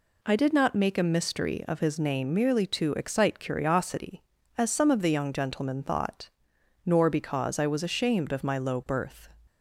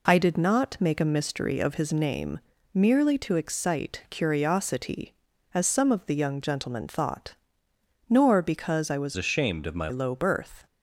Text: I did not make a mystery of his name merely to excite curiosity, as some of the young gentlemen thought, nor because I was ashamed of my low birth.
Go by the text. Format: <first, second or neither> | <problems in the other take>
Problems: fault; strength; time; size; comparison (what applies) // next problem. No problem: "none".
first | pauses between "name" and "merely"; slight; at 2.3 s; 0.34 s long // changes voice from "ashamed" to "my"; from 9.1 to 9.8 s; 0.7 s long